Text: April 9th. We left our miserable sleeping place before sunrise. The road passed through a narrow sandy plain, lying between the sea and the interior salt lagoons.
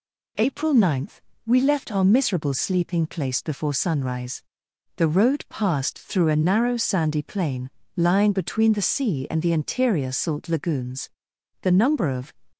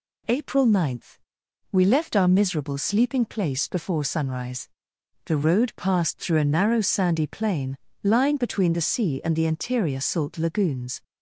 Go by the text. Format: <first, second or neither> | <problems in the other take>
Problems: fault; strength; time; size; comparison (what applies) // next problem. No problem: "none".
second | goes on to say "The number of"; noticeable; from 11.6 s on; 0.74 s long